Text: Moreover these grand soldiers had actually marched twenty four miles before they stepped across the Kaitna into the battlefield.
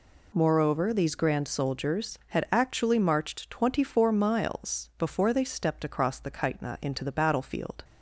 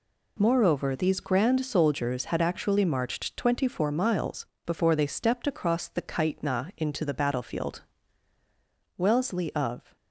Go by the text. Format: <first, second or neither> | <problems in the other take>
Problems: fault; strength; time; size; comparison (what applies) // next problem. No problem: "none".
first | pauses between "miles" and "before"; slight; at 4.4 s; 0.20 s long // goes on to say "Wellesley of"; noticeable; from 8.9 s on; 0.98 s long